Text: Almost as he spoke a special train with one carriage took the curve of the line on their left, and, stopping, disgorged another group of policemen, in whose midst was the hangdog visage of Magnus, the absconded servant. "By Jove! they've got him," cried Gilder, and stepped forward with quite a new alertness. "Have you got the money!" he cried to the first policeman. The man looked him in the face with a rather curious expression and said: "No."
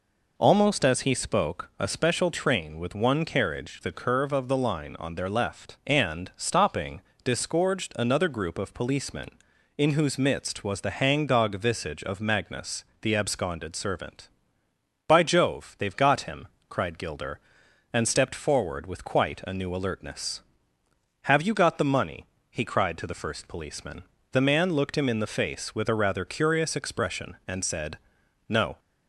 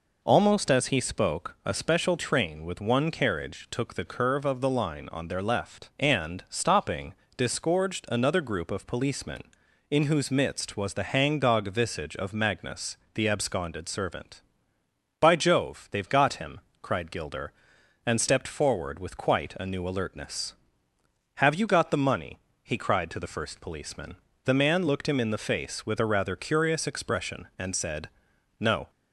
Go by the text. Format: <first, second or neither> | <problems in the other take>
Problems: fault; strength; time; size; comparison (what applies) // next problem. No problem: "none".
second | skips "took"; at 3.8 s